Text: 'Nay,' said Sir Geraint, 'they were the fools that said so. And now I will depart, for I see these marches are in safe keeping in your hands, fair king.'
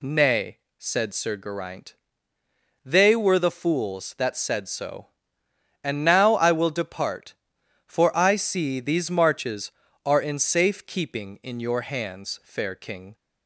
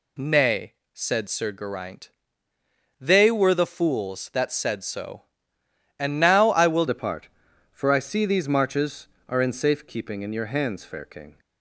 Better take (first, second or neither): first